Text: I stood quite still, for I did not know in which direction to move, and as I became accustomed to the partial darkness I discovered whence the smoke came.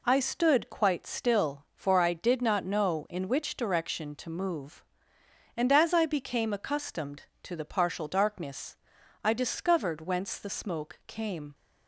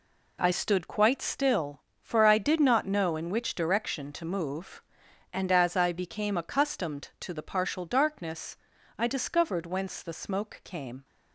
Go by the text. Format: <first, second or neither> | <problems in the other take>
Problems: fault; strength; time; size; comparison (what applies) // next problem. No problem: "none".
neither | pauses between "darkness" and "I"; the same in both